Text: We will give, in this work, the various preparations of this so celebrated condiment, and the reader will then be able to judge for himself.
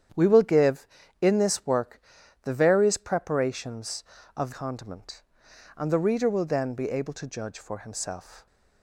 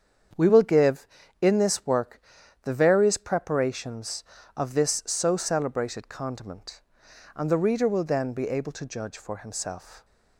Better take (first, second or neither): second